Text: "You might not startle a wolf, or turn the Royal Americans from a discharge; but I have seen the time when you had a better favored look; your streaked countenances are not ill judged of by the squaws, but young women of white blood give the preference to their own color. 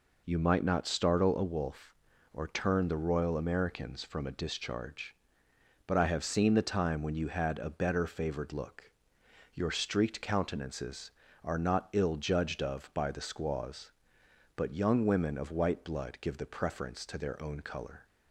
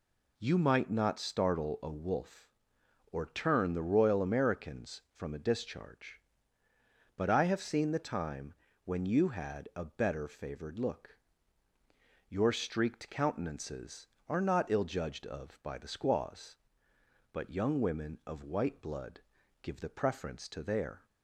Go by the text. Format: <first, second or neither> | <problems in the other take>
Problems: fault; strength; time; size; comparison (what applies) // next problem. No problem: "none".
first | pauses between "time" and "when"; slight; at 8.5 s; 0.30 s long // pauses between "blood" and "give"; at 19.2 s; 0.40 s long // stops before "own color"; at 21.0 s